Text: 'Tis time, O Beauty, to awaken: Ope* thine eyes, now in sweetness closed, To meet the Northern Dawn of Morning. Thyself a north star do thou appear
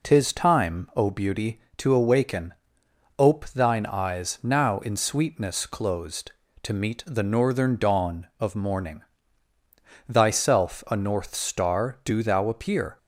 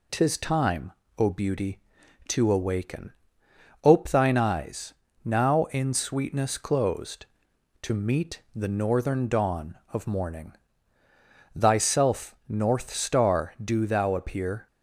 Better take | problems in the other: first | skips "a"; at 12.4 s

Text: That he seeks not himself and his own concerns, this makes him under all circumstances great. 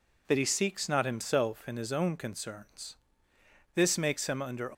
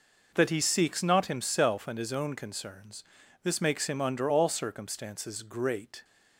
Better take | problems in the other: second | stops before "all circumstances great"; at 4.7 s

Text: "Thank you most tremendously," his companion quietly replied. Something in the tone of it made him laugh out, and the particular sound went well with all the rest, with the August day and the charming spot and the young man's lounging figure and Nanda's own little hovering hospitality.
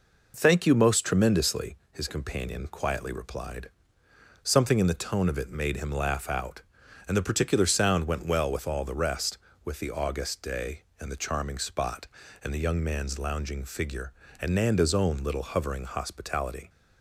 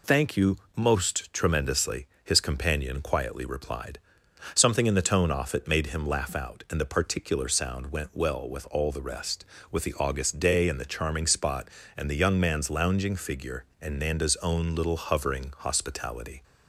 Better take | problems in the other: first | pauses between "you" and "most"; slight; at 0.5 s; 0.18 s long // says "off" for "of"; at 5.3 s

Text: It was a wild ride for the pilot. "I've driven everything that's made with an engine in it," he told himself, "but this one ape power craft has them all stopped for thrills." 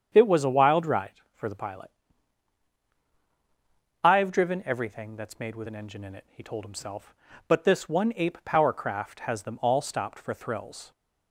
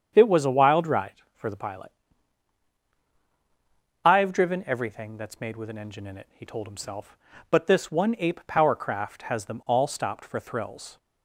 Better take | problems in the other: neither | starts louder than the rest; strong; the same in both

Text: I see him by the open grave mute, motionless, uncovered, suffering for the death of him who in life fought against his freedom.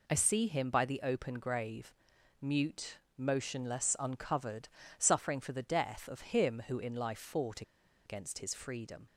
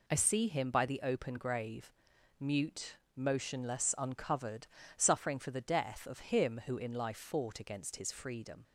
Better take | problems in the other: second | pauses between "grave" and "mute"; noticeable; at 1.9 s; 0.48 s long; noticeable in the second // pauses between "fought" and "against"; at 7.6 s; 0.43 s long

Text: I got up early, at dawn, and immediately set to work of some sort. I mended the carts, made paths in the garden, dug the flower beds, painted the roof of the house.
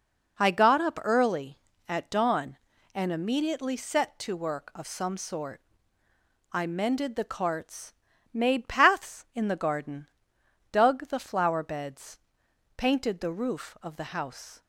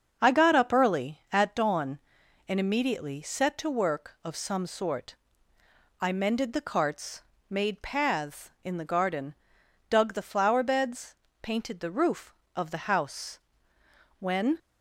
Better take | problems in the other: first | starts louder than the rest; until 1.2 s; 6.5 dB // goes on to say "When"; slight; from 14.1 s on; 0.40 s long

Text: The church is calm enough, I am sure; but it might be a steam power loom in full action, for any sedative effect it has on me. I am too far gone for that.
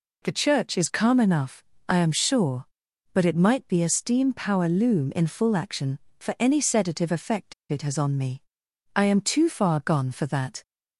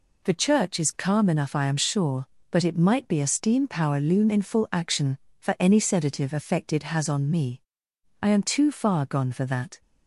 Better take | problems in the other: second | pauses between "effect" and "it"; slight; at 7.5 s; 0.18 s long

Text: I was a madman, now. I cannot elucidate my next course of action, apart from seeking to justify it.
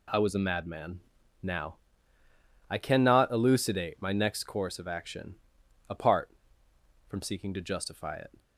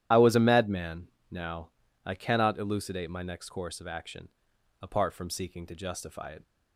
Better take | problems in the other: first | loses the start of "I"; at 0.1 s; 35 ms // starts louder than the rest; strong; until 1.3 s; 11 dB

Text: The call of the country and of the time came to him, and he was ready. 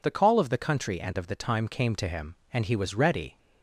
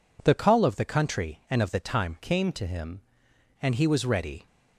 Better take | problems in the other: first | changes voice from "came" to "him"; from 2.2 to 3.0 s; 0.8 s long

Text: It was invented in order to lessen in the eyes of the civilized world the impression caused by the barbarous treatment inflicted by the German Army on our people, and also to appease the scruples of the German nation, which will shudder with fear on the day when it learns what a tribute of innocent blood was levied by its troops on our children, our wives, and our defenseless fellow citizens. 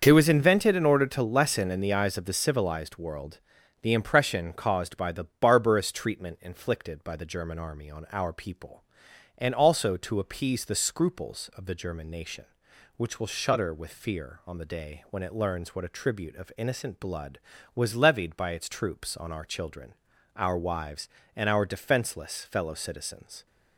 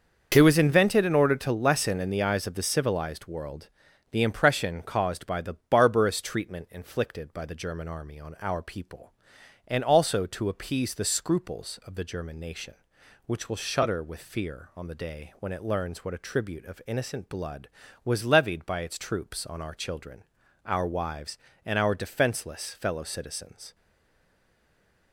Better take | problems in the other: first | starts louder than the rest; until 1.3 s; 6.5 dB; also in the first // pauses between "world" and "the"; at 3.6 s; 0.40 s long; also in the first // stays silent after the last word; noticeable; from 23.7 s on; 1.4 s long

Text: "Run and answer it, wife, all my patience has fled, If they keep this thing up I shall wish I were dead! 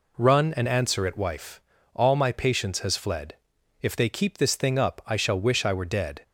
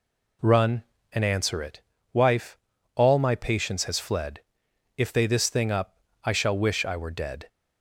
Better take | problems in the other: first | skips "keep"; at 5.2 s // pauses between "up" and "I"; slight; at 5.9 s; 0.26 s long

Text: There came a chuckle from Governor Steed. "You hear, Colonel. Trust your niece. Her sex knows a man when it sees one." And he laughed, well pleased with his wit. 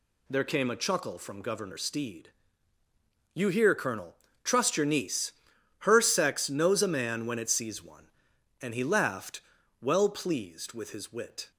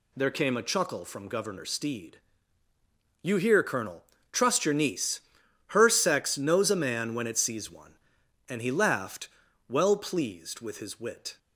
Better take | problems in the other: neither | none

